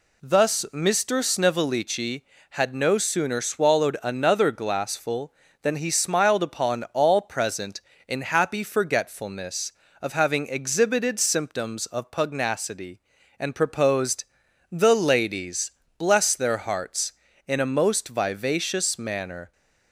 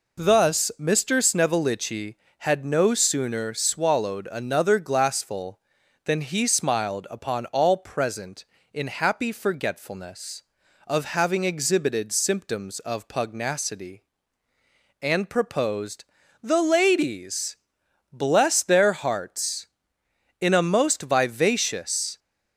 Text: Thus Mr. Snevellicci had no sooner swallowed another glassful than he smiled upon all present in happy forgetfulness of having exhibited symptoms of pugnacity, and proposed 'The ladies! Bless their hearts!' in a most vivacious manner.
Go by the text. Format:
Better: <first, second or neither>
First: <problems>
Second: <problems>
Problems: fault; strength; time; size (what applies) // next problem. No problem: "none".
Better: first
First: pauses between "proposed" and "The"; at 14.2 s; 0.44 s long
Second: pauses between "proposed" and "The"; at 16.0 s; 0.40 s long // stops before "manner"; at 22.1 s